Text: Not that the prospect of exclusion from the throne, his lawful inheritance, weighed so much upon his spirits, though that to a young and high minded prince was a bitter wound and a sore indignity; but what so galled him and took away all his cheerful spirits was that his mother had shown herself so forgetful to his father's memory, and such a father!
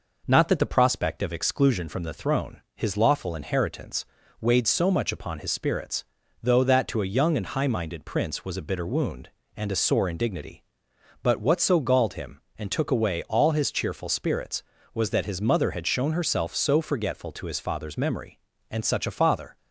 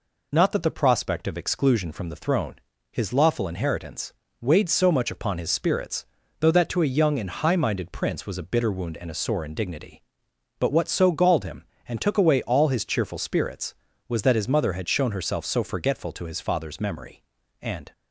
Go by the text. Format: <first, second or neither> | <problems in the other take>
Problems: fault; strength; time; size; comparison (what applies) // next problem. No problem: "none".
first | stops before "such a father"; at 17.9 s